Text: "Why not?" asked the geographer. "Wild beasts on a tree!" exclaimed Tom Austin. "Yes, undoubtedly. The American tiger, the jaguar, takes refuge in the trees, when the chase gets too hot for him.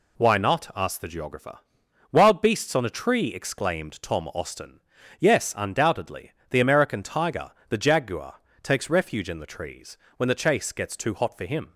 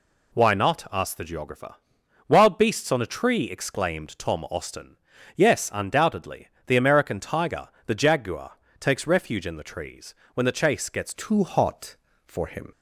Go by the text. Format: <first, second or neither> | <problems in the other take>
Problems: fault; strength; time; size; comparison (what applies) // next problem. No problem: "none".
first | changes voice at "too"; from 11.1 s on; 1.6 s long